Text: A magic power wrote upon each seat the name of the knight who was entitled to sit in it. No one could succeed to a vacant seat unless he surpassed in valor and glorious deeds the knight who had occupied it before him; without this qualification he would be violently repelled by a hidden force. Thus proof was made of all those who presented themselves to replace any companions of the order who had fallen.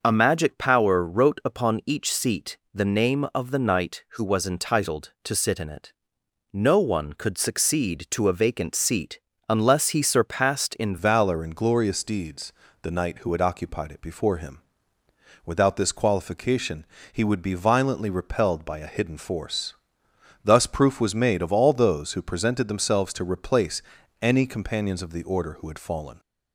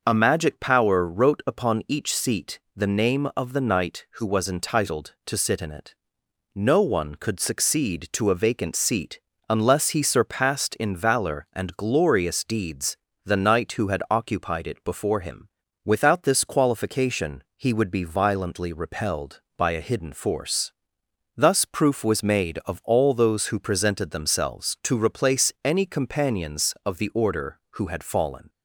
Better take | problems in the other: second | starts louder than the rest; noticeable; until 1.0 s; 6 dB; noticeable in the second // pauses between "seat" and "the"; slight; at 2.5 s; 0.16 s long; slight in the second // pauses between "seat" and "unless"; slight; at 9.1 s; 0.28 s long; slight in the second // changes voice at "valor"; from 10.9 s on; 15.2 s long // pauses between "deeds" and "the"; slight; at 12.5 s; 0.28 s long; slight in the second // pauses between "qualification" and "he"; slight; at 16.8 s; 0.26 s long // pauses between "replace" and "any"; at 23.8 s; 0.40 s long

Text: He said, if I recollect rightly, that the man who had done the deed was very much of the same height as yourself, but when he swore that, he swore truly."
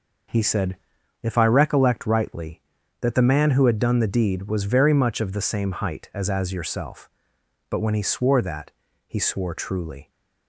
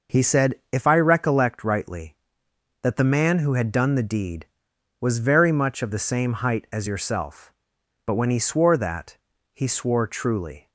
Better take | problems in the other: second | says "as" twice; at 6.2 s

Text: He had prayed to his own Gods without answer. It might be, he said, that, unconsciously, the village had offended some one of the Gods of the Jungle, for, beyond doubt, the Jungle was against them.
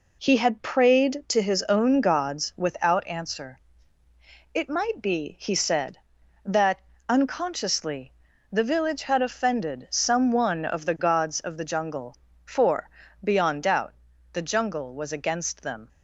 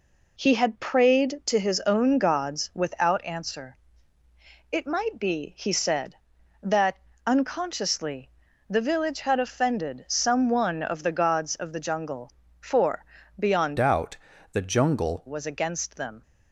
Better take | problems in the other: first | changes voice from "doubt" to "Jungle"; from 13.7 to 15.2 s; 1.5 s long

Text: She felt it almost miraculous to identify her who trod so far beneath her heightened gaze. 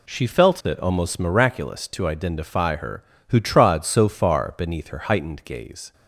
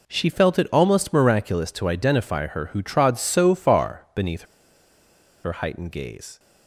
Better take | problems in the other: first | pauses between "beneath" and "her"; at 4.4 s; 1.0 s long

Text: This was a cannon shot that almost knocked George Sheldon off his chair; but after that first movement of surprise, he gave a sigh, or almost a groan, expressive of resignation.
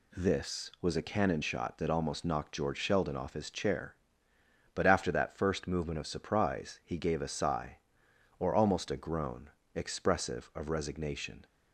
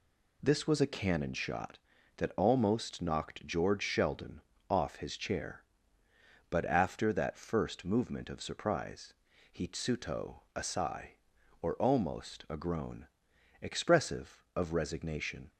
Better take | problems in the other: first | pauses between "Sheldon" and "off"; slight; at 4.3 s; 0.30 s long // says "tsuto" for "gave"; at 9.6 s

